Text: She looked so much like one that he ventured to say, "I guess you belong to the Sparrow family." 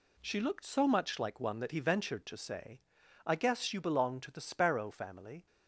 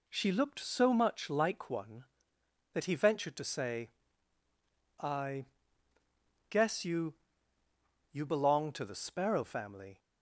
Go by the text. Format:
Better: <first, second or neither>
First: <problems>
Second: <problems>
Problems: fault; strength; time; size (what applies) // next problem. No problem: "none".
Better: first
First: none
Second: pauses between "I" and "guess"; at 5.4 s; 1.0 s long // says "you" twice; at 8.1 s